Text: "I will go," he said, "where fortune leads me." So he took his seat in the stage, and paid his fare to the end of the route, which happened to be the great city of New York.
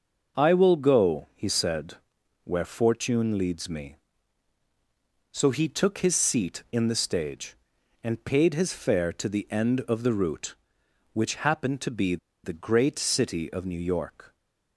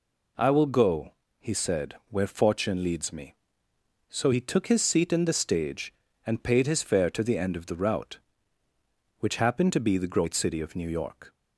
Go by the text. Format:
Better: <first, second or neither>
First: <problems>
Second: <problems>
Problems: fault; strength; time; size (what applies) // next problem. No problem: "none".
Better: second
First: starts louder than the rest; until 1.4 s; 6.5 dB // pauses between "be" and "the"; slight; at 12.1 s; 0.27 s long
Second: none